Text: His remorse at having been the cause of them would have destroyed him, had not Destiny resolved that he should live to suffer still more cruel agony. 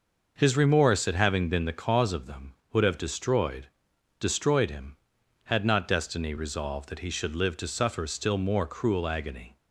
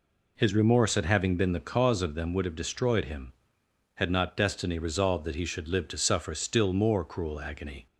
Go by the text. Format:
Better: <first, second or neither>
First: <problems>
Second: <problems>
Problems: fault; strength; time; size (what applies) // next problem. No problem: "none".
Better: second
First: says "destroyed" twice; at 4.1 s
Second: none